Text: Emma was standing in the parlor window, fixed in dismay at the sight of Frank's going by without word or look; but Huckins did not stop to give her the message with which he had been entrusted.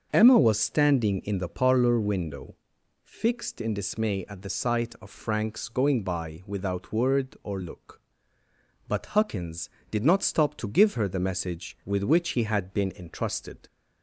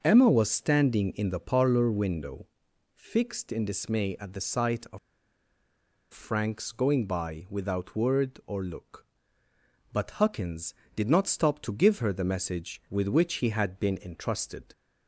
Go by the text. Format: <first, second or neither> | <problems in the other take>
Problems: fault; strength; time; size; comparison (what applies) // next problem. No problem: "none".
first | starts louder than the rest; until 1.0 s; 6.5 dB; also in the first // pauses between "of" and "Frank's"; at 4.9 s; 1.1 s long